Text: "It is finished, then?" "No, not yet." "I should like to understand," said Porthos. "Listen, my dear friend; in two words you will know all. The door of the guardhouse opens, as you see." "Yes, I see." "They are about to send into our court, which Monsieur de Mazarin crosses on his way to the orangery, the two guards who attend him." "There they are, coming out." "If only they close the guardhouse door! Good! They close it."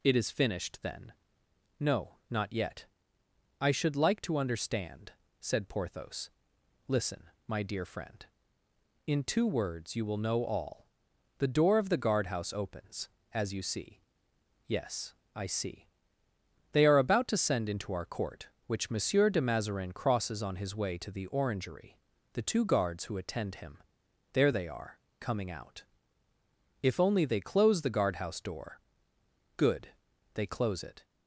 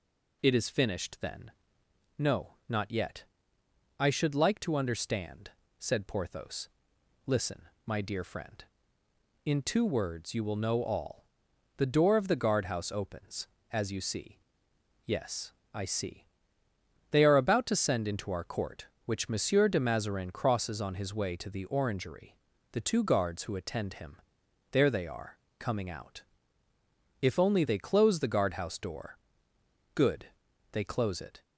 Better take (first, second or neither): neither